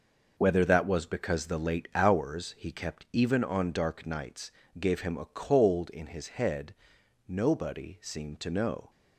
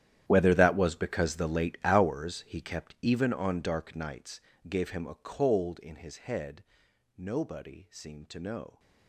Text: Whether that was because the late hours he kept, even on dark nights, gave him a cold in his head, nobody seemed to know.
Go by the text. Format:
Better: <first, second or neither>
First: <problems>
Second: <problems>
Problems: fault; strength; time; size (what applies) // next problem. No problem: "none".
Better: first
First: none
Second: gets quieter; strong; throughout; 17.5 dB